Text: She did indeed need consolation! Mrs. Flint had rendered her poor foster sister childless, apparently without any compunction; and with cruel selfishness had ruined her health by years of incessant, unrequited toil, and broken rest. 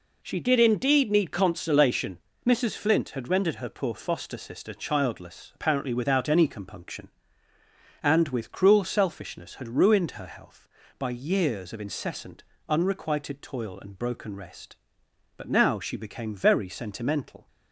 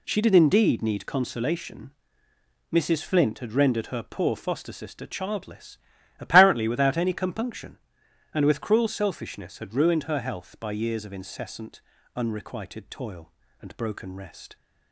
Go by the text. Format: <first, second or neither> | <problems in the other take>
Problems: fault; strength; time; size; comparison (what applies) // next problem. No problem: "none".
second | goes on to say "But now she became very sentimental"; strong; from 15.3 s on; 2.1 s long